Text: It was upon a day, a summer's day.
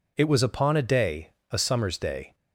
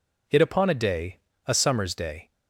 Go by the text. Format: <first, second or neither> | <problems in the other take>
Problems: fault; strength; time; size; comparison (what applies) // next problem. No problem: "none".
first | skips "was"; at 0.4 s